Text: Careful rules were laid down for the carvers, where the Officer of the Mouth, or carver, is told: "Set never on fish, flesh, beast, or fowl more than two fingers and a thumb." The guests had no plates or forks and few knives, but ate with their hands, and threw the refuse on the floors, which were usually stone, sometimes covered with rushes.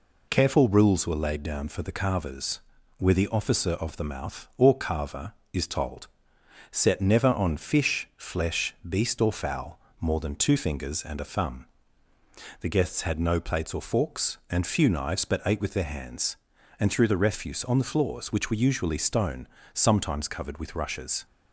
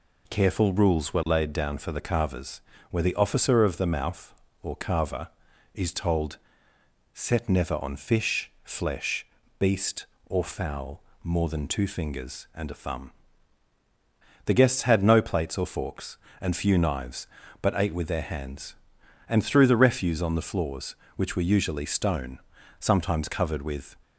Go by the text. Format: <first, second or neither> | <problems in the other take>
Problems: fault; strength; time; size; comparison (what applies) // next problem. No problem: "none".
first | pauses between "fowl" and "more"; slight; at 11.0 s; 0.22 s long; slight in the first // stops before "rushes"; at 24.0 s